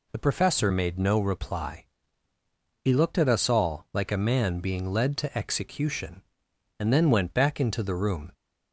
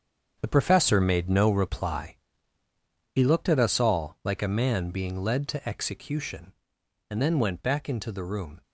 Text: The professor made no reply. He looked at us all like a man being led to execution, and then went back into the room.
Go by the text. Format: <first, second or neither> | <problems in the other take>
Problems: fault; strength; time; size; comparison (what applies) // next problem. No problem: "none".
first | gets quieter; strong; throughout; 9 dB